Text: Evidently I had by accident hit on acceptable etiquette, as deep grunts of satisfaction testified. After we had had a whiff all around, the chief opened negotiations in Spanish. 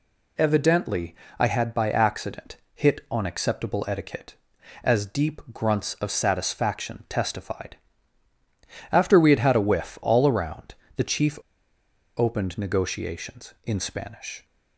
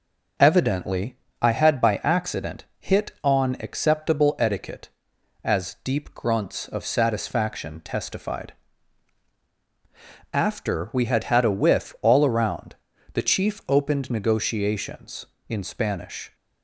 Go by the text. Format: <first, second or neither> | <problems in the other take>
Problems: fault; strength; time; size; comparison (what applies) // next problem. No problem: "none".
second | pauses between "Evidently" and "I"; slight; at 1.1 s; 0.24 s long; slight in the second // pauses between "accident" and "hit"; slight; at 2.5 s; 0.18 s long // pauses between "chief" and "opened"; noticeable; at 11.3 s; 0.78 s long